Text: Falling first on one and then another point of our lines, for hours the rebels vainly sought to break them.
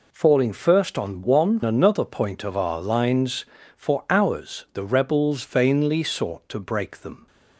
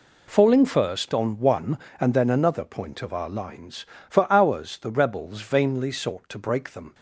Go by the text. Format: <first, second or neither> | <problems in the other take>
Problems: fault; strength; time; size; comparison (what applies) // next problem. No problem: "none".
second | skips "and then"; at 1.6 s